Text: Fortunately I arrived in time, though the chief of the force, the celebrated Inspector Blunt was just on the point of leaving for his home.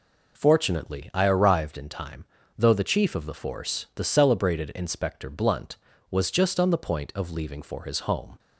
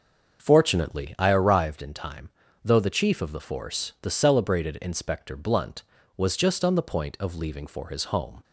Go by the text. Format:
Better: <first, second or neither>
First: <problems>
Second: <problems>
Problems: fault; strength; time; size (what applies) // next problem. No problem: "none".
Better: first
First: none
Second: starts louder than the rest; until 1.5 s; 6.5 dB